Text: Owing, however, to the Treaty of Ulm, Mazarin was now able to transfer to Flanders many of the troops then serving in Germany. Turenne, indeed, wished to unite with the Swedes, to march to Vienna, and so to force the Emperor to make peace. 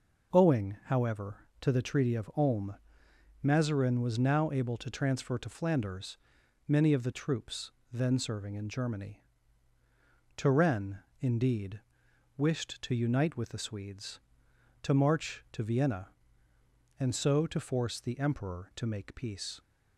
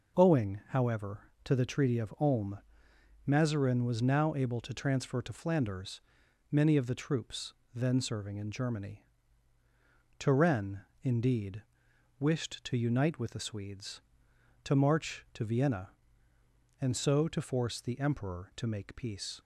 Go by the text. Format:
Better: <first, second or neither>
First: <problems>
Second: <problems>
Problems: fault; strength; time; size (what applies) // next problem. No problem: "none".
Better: neither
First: pauses between "Flanders" and "many"; noticeable; at 6.1 s; 0.52 s long // pauses between "troops" and "then"; slight; at 7.6 s; 0.22 s long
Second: pauses between "Flanders" and "many"; noticeable; at 6.0 s; 0.52 s long // pauses between "troops" and "then"; slight; at 7.5 s; 0.22 s long